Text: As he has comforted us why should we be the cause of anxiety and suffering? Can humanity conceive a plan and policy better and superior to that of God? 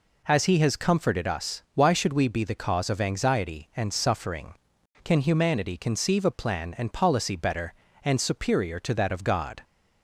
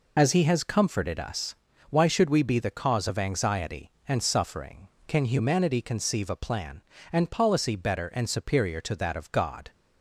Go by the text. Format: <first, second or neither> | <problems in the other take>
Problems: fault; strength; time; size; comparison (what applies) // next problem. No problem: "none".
first | loses the start of "As"; at 0.1 s; 30 ms // pauses between "us" and "why"; slight; at 1.5 s; 0.33 s long